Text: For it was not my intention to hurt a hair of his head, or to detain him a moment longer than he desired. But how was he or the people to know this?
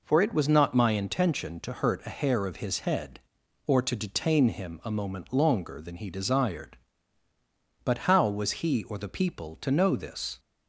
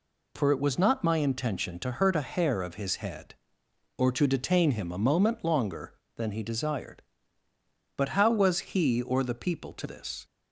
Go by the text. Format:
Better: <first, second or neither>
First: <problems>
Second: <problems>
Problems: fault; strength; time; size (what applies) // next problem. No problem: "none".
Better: first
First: none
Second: skips "know"; at 9.8 s